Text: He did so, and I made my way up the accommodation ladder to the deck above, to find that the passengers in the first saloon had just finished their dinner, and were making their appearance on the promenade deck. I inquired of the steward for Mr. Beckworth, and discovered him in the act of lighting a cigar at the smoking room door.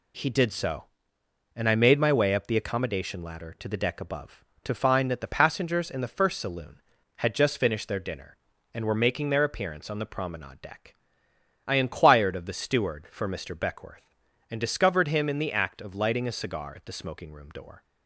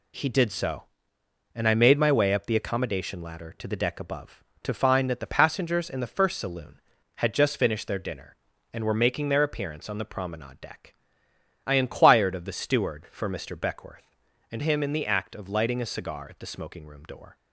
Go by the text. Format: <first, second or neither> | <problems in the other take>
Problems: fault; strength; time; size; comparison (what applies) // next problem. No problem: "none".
first | skips "discovered"; at 14.6 s